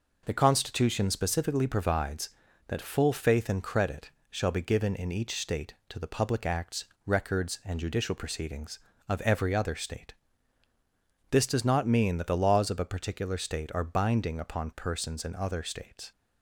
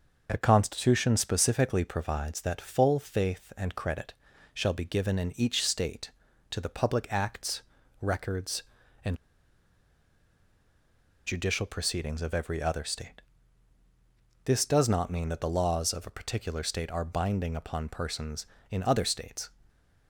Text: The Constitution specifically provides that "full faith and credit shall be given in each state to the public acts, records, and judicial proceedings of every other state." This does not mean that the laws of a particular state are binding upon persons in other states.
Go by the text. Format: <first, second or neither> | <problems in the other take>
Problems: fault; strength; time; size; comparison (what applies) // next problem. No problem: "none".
first | pauses between "credit" and "shall"; at 4.1 s; 0.42 s long; slight in the first // pauses between "and" and "judicial"; strong; at 9.1 s; 2.0 s long